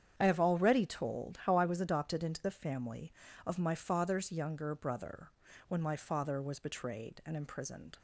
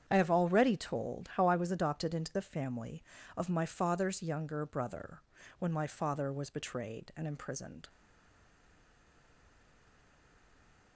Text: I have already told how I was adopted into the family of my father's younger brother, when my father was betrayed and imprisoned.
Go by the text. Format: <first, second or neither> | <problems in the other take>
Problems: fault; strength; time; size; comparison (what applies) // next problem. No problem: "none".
first | starts louder than the rest; strong; until 1.0 s; 8.5 dB; strong in the first // stays silent after the last word; strong; from 7.8 s on; 3.1 s long